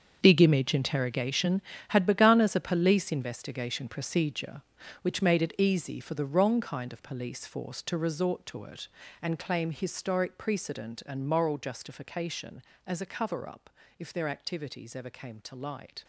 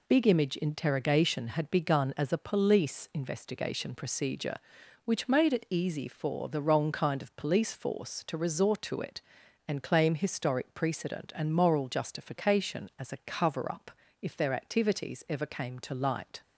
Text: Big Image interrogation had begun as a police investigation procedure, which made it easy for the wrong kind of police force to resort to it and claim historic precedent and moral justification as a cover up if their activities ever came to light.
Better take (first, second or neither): second